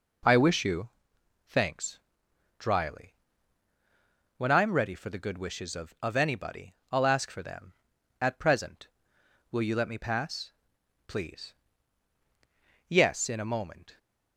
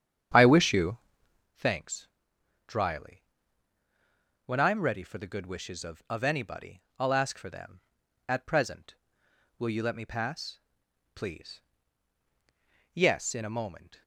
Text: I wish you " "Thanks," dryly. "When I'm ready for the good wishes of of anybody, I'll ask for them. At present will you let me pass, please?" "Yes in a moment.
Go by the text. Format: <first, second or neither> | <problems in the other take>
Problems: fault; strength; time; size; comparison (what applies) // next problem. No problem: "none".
first | starts louder than the rest; strong; until 1.5 s; 8.5 dB